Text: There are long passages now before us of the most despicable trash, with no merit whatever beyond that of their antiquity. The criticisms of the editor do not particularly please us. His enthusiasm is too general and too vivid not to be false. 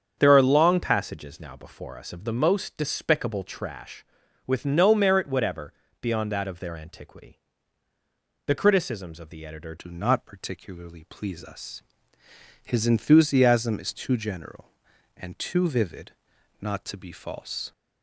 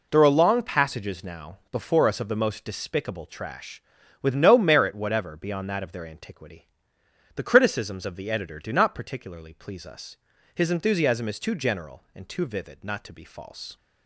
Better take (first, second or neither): second